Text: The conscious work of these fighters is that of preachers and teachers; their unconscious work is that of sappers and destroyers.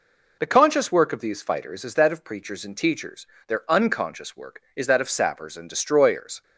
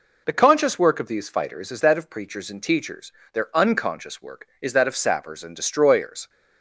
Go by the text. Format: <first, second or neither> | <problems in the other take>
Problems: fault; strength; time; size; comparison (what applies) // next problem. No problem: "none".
neither | none